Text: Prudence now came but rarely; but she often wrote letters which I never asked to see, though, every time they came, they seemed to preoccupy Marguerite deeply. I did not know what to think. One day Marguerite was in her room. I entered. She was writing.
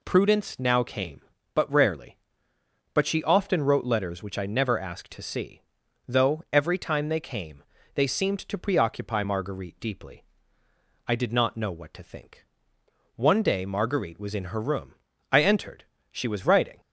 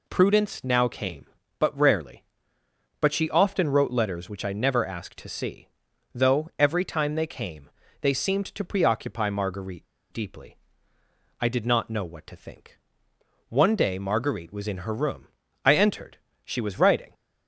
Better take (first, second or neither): first